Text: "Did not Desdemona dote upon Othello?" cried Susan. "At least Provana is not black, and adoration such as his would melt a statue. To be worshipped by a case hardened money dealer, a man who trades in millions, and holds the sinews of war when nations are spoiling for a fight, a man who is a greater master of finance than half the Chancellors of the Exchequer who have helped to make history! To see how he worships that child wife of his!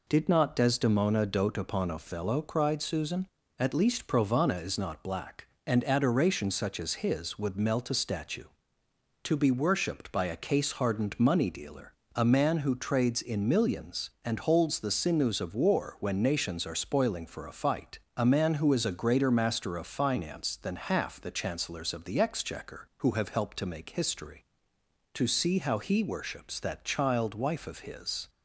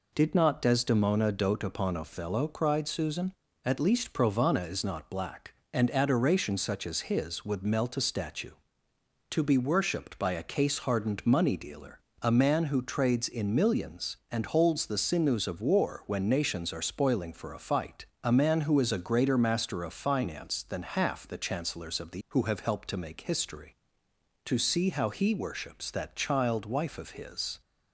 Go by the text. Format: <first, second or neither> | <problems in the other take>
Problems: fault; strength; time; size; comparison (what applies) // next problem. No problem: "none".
first | skips "Exchequer"; at 22.2 s